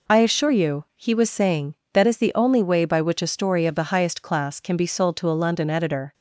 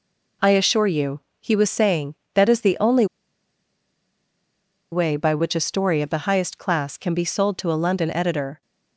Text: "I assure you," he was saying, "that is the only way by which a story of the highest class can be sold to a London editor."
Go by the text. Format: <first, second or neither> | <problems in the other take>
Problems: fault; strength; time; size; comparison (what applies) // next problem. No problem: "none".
first | pauses between "only" and "way"; strong; at 3.0 s; 1.8 s long